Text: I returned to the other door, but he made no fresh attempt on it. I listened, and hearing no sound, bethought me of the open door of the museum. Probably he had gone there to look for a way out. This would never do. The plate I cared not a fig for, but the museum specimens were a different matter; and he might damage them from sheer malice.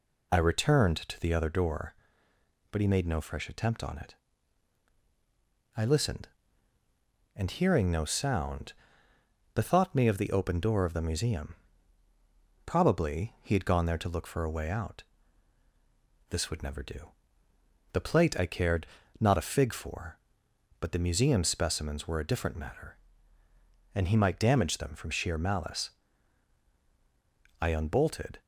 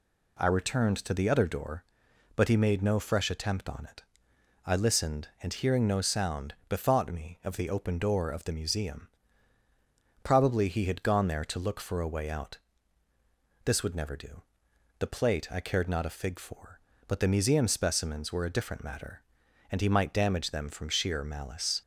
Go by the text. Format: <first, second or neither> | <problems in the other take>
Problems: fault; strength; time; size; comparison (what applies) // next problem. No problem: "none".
second | pauses between "cared" and "not"; slight; at 18.8 s; 0.34 s long // goes on to say "I unbolted"; noticeable; from 27.6 s on; 0.78 s long